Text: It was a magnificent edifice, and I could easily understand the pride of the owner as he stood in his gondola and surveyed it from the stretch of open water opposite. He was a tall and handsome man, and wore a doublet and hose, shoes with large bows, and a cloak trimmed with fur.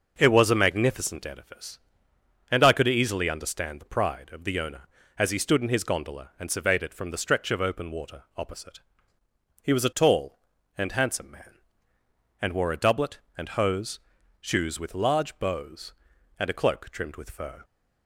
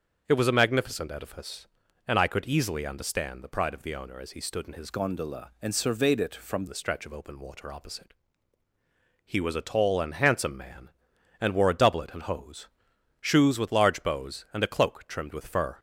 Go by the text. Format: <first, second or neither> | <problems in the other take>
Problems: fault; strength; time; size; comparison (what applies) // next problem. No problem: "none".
first | starts louder than the rest; until 1.2 s; 6.5 dB // changes voice from "gondola" to "from"; from 4.8 to 6.6 s; 1.8 s long